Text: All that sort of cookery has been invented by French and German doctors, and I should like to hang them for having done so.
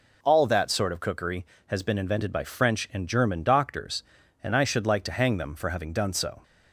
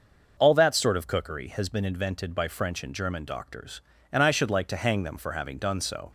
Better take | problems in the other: neither | none

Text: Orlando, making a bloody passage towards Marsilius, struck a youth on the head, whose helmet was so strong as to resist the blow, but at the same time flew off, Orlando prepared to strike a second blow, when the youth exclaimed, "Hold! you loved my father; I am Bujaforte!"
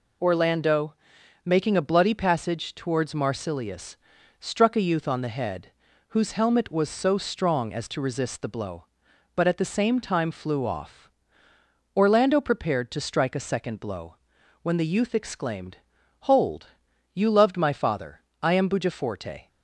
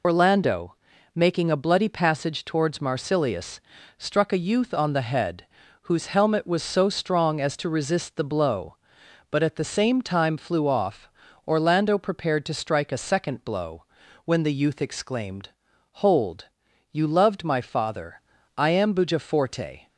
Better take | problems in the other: first | loses the start of "Orlando"; at 0.0 s; 50 ms

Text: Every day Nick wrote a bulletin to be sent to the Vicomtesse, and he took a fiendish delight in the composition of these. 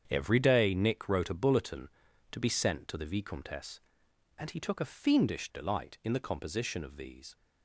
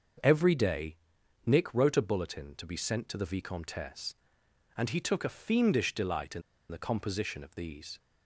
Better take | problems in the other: first | starts louder than the rest; until 1.7 s; 6.5 dB; strong in the first // pauses between "day" and "Nick"; noticeable; at 0.9 s; 0.50 s long // pauses between "in" and "the"; slight; at 6.4 s; 0.28 s long

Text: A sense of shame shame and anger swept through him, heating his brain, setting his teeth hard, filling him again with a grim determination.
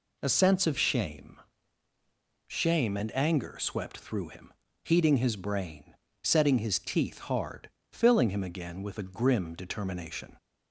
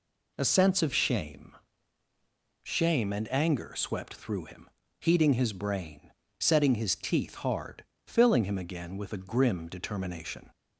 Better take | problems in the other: neither | pauses between "shame" and "shame"; the same in both

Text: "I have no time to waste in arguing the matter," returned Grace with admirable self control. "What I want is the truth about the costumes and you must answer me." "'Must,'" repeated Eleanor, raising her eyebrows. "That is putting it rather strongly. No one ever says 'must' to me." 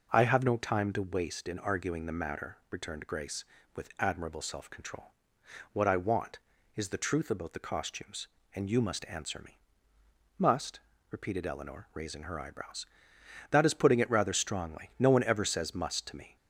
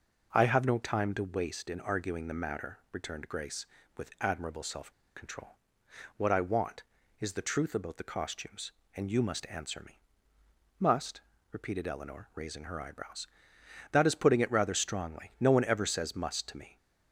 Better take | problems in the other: first | pauses between "self" and "control"; slight; at 4.9 s; 0.23 s long

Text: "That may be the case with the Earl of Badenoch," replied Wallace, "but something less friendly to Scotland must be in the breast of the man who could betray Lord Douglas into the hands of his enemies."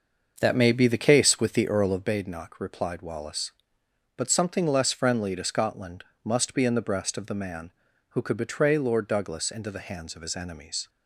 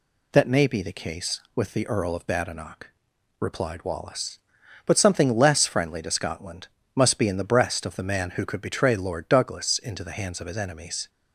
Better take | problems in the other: second | starts louder than the rest; until 2.2 s; 6.5 dB // pauses between "Scotland" and "must"; slight; at 6.0 s; 0.22 s long; slight in the second

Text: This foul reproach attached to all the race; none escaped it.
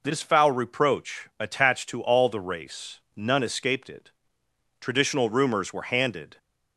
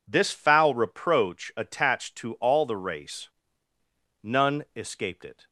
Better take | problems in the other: second | goes on to say "Traditional rumors were handed"; from 4.7 s on; 1.5 s long

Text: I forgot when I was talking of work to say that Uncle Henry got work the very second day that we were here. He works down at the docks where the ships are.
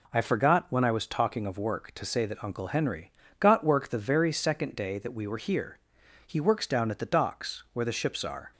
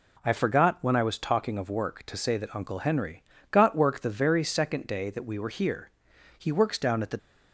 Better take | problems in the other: first | pauses between "Henry" and "got"; slight; at 3.2 s; 0.30 s long; slight in the first // stops before "docks where the ships are"; at 7.1 s

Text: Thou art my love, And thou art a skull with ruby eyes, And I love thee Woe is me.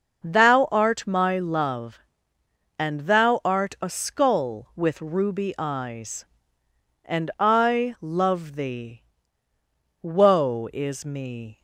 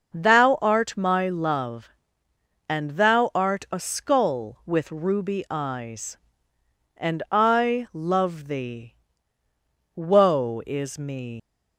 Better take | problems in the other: first | starts louder than the rest; noticeable; until 1.1 s; 6 dB; noticeable in the first // pauses between "thee" and "Woe"; at 8.9 s; 1.0 s long; also in the first // leaves "me" unfinished; at 11.3 s; 150 ms

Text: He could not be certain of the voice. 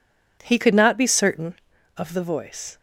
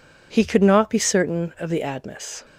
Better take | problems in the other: first | says "admis" for "voice"; at 1.8 s

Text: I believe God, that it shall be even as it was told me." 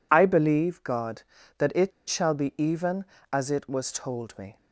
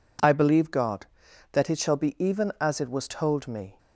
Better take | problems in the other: second | pauses between "it" and "shall"; slight; at 1.9 s; 0.17 s long

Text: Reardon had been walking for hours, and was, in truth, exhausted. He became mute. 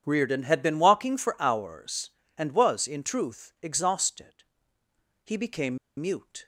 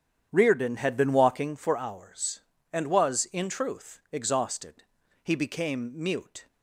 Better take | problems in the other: second | starts louder than the rest; strong; until 1.0 s; 8.5 dB; strong in the second // pauses between "became" and "mute"; slight; at 5.7 s; 0.21 s long

